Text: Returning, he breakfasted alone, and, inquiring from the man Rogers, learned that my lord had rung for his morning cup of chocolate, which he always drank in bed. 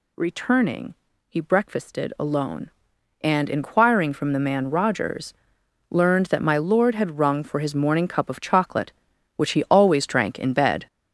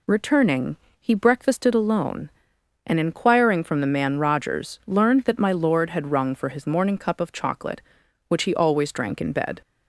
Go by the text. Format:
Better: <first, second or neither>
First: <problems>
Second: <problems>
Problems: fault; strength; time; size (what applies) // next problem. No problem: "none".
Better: second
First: gets louder; noticeable; throughout; 5.5 dB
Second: none